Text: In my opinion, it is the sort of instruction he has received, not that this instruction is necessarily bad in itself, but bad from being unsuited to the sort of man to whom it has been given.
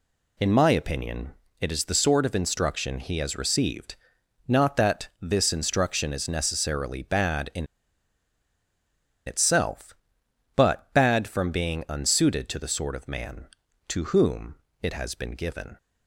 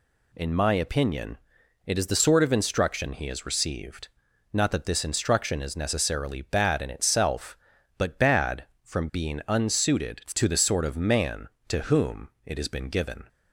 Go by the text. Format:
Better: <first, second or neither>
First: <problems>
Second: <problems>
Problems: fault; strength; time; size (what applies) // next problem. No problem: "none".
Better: second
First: pauses between "in" and "itself"; strong; at 7.6 s; 1.6 s long // pauses between "whom" and "it"; slight; at 14.5 s; 0.26 s long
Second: pauses between "whom" and "it"; slight; at 12.2 s; 0.16 s long